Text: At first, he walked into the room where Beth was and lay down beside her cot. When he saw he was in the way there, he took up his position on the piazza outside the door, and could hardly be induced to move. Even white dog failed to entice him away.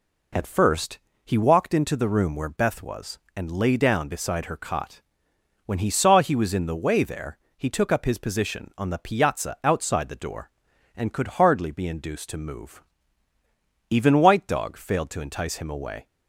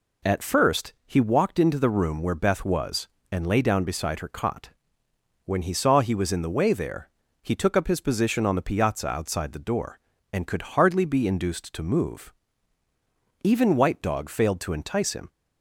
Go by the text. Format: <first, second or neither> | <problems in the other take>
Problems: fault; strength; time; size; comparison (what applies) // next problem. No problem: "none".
first | stops before "away"; at 15.2 s